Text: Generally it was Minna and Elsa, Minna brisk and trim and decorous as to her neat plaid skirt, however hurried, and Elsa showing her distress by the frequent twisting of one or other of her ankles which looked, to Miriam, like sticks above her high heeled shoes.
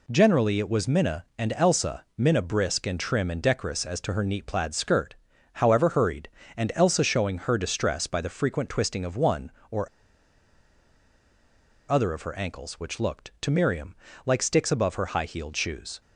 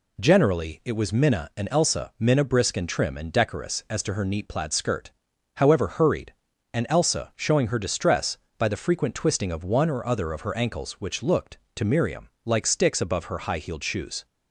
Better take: second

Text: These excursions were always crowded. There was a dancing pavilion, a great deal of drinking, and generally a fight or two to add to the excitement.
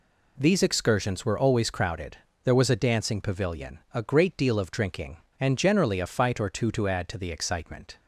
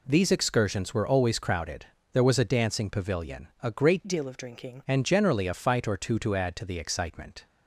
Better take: first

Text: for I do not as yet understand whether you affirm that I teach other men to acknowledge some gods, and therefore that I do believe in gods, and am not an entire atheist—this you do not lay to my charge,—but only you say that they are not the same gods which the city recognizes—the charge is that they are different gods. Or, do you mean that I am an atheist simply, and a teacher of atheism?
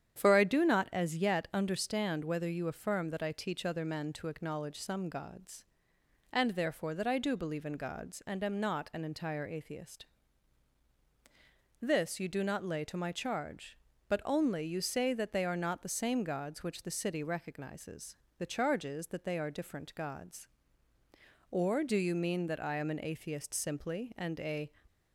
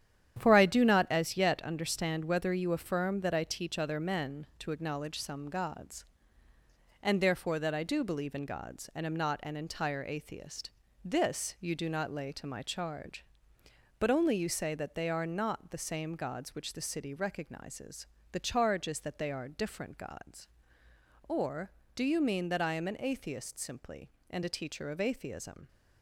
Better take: second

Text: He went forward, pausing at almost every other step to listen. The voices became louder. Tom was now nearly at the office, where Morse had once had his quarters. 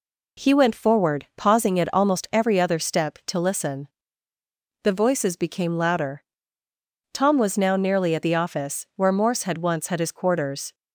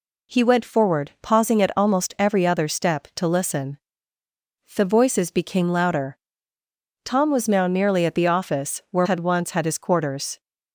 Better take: first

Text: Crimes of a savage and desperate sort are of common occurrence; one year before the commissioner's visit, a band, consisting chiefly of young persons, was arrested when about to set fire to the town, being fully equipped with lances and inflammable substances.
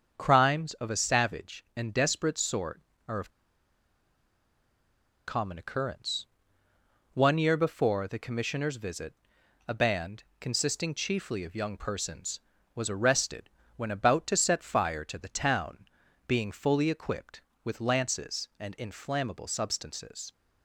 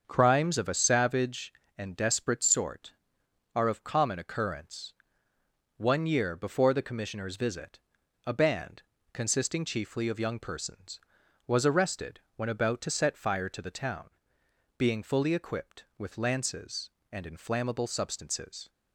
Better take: second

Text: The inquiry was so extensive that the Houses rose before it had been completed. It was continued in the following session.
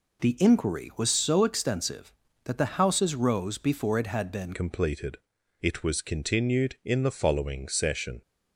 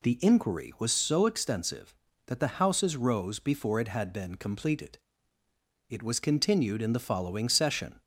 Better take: second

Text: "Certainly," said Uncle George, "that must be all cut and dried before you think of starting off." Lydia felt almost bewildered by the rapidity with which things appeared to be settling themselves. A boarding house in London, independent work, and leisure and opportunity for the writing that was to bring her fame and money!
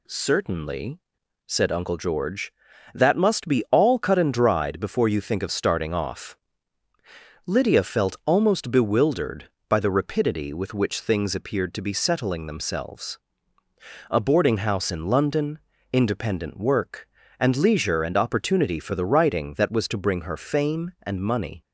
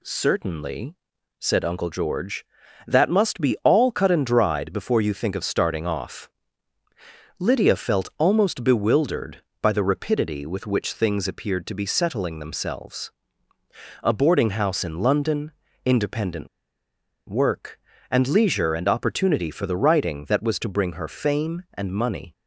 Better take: first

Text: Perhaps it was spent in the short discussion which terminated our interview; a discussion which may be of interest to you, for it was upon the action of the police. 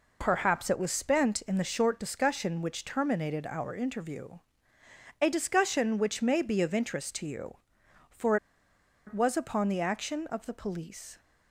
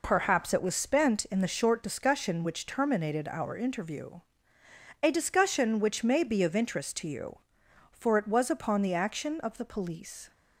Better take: second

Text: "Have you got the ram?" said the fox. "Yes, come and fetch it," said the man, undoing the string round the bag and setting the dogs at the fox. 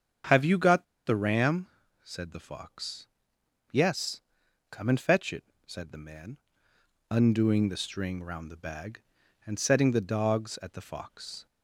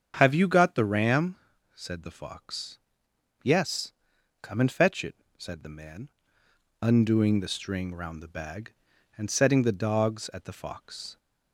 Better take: second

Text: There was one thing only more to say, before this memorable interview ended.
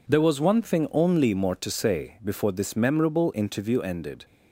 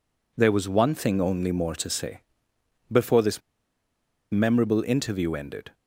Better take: first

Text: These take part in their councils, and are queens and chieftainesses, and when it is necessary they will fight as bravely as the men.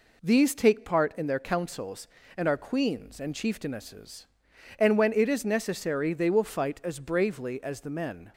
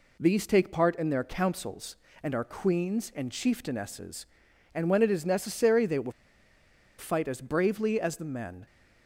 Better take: first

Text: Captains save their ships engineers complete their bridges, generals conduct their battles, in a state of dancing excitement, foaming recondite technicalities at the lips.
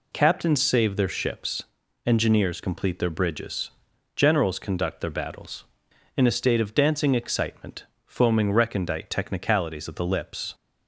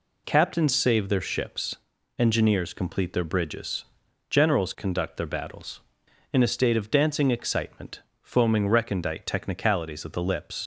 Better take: first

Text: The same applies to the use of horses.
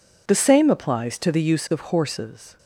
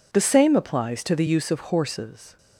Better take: neither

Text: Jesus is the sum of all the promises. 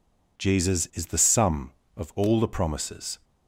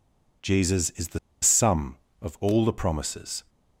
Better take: first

